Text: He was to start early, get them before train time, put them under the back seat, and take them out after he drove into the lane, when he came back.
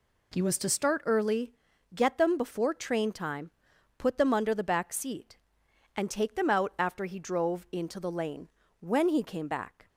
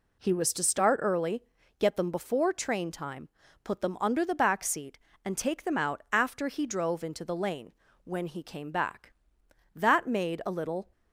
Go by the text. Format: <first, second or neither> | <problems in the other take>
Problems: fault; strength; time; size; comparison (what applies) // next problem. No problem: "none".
first | goes on to say "That made a little"; noticeable; from 9.7 s on; 1.1 s long